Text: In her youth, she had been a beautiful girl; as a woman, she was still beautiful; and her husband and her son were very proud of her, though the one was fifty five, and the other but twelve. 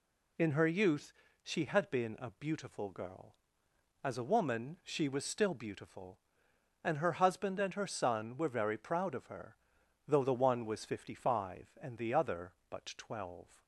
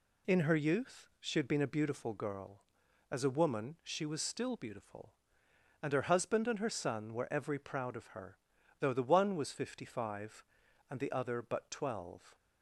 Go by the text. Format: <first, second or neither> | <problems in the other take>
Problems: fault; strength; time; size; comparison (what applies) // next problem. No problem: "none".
first | says "every" for "very"; at 7.2 s